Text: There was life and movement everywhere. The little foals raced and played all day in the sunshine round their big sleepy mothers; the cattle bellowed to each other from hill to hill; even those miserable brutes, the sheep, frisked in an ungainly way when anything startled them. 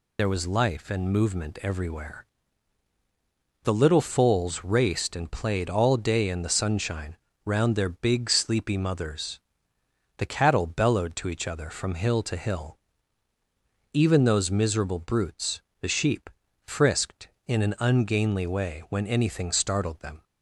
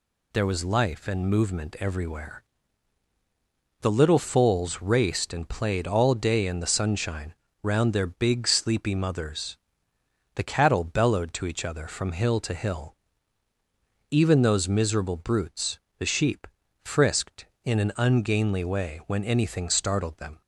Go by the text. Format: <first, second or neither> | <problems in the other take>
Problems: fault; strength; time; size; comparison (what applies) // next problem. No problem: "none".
second | loses the start of "There"; at 0.1 s; 40 ms // pauses between "sunshine" and "round"; slight; at 7.1 s; 0.30 s long; slight in the second